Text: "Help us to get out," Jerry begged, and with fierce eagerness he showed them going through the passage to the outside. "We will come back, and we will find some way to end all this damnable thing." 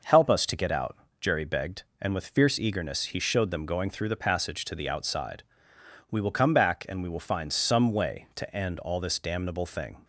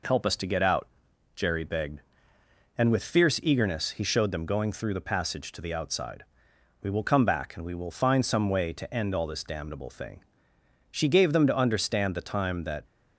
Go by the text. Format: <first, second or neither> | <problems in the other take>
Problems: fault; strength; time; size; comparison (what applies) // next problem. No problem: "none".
first | goes on to say "She gave them to understand the time that"; strong; from 10.9 s on; 1.9 s long